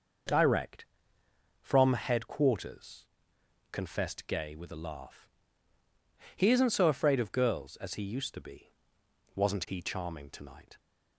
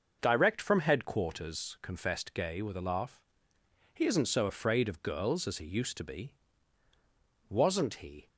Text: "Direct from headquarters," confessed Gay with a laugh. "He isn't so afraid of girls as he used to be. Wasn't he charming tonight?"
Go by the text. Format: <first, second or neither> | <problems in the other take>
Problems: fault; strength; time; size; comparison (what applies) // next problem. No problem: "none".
first | stops before "charming tonight"; at 8.2 s